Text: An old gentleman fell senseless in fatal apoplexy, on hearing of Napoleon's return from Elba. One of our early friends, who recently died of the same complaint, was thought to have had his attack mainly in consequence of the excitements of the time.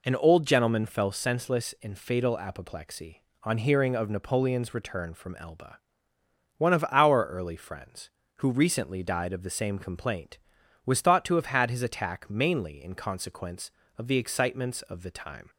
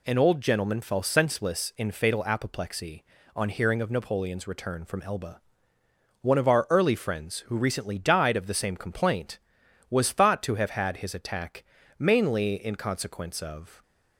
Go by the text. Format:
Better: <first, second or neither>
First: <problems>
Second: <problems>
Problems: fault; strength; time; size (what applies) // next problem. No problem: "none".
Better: first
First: none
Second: pauses between "attack" and "mainly"; slight; at 11.6 s; 0.36 s long // stops before "the excitements of the time"; at 13.8 s